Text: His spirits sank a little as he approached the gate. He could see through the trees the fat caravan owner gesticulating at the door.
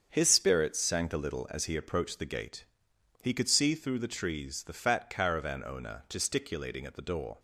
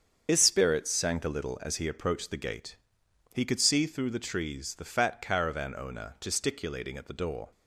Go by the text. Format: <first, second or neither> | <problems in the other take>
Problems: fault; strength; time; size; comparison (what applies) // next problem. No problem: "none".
first | loses the start of "His"; at 0.2 s; 70 ms // starts louder than the rest; strong; until 1.2 s; 7 dB; strong in the first